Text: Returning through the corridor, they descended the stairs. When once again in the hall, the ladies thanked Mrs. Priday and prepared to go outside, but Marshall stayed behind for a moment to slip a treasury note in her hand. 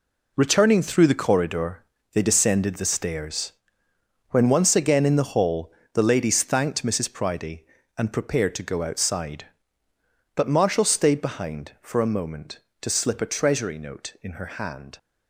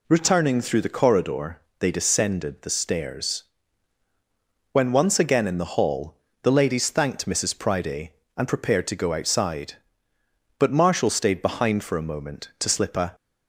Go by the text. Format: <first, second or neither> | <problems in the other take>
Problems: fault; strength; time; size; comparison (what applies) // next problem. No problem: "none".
first | stops before "treasury note in her hand"; at 13.1 s